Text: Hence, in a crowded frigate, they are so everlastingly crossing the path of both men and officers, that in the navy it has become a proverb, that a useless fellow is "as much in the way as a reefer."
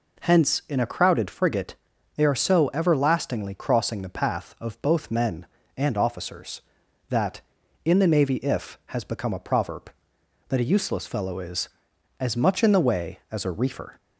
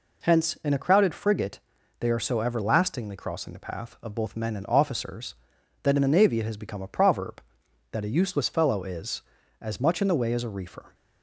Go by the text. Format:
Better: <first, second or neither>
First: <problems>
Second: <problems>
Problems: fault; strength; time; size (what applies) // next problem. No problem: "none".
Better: second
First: says "if" for "it"; at 8.3 s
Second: none